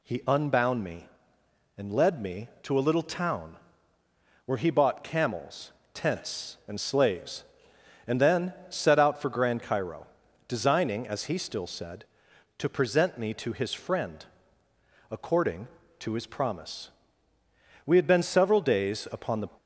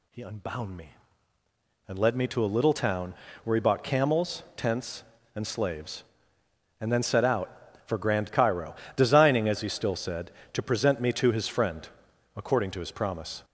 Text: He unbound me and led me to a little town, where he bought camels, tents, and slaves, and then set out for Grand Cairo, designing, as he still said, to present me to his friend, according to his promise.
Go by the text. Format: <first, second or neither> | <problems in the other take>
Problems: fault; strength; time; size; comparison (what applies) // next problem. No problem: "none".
second | pauses between "then" and "set"; slight; at 8.5 s; 0.16 s long // goes on to say "We had been several days upon the"; from 17.8 s on; 1.6 s long